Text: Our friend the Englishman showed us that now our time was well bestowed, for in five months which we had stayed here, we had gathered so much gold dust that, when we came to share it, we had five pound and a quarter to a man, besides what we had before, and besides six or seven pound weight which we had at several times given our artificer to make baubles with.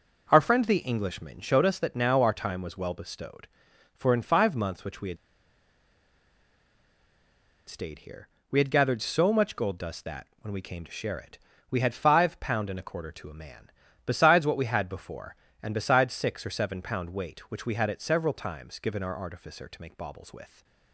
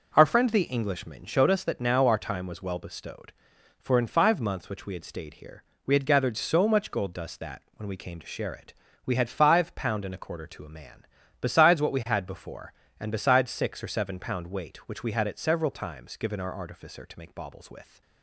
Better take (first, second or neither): second